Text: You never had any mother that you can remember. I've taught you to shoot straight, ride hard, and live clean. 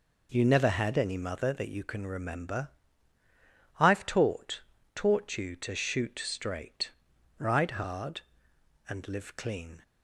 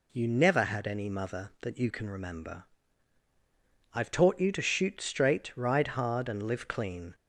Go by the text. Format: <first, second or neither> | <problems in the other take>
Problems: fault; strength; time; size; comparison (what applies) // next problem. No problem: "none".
second | says "taught" twice; at 4.9 s